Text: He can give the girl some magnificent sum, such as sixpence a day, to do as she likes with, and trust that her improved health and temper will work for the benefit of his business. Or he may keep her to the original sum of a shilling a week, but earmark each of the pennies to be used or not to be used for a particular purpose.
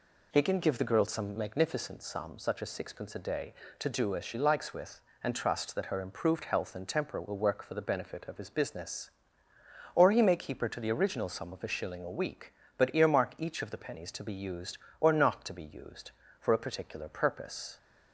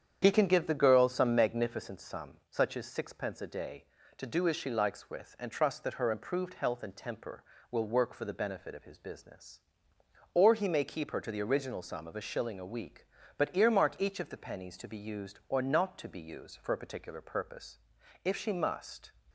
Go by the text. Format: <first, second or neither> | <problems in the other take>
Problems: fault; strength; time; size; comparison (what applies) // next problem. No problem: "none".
first | starts louder than the rest; strong; until 1.2 s; 8.5 dB // goes on to say "If she must"; noticeable; from 18.2 s on; 0.86 s long